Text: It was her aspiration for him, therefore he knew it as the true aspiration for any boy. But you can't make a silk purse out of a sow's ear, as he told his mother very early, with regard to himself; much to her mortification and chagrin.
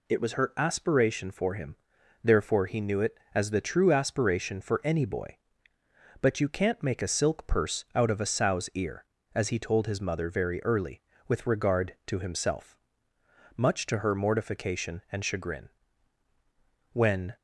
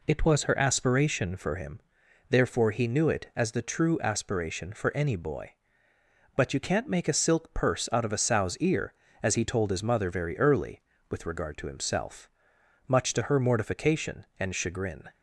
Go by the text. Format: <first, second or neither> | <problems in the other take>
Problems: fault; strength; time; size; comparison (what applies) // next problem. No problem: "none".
second | goes on to say "When"; slight; from 16.9 s on; 0.44 s long